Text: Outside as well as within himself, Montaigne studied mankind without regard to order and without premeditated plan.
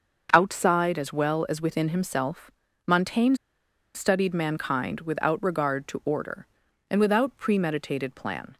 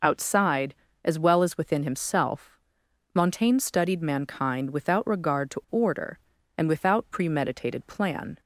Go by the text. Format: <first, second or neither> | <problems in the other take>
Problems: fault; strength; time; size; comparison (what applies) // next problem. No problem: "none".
second | starts louder than the rest; until 1.3 s; 6.5 dB // pauses between "Montaigne" and "studied"; noticeable; at 3.3 s; 0.60 s long